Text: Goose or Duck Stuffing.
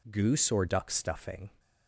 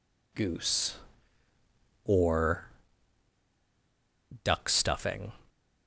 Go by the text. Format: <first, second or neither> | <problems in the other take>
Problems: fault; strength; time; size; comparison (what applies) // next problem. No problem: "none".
first | pauses between "or" and "Duck"; strong; at 2.7 s; 1.7 s long